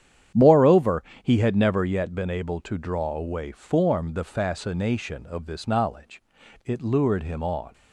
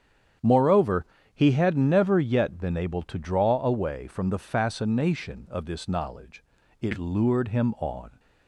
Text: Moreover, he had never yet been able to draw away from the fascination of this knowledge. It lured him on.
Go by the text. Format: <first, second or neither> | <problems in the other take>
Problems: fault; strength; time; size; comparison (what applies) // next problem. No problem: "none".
second | starts louder than the rest; strong; until 1.5 s; 9.5 dB; strong in the second // says "form" for "from"; at 3.5 s